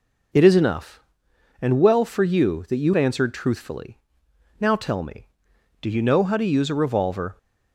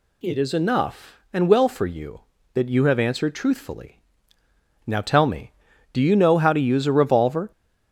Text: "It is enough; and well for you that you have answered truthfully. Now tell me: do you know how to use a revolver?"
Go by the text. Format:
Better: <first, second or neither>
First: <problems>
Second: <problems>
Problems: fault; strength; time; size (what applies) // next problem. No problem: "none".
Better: second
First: skips "have"; at 2.9 s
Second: none